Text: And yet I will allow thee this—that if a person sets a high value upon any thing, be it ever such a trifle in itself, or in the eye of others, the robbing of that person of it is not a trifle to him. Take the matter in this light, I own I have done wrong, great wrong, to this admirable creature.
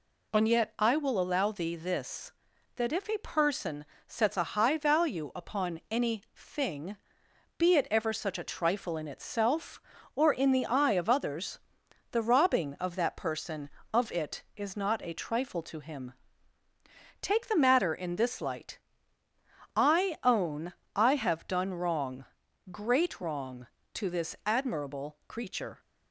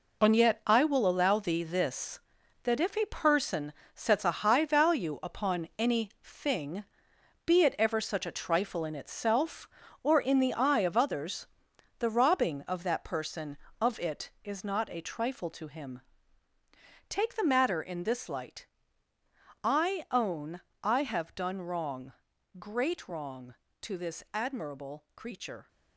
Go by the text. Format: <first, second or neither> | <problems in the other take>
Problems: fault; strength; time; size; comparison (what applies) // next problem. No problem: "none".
first | gets quieter; strong; throughout; 9 dB // pauses between "person" and "sets"; slight; at 3.7 s; 0.22 s long; slight in the first // pauses between "own" and "I"; slight; at 20.5 s; 0.22 s long; slight in the first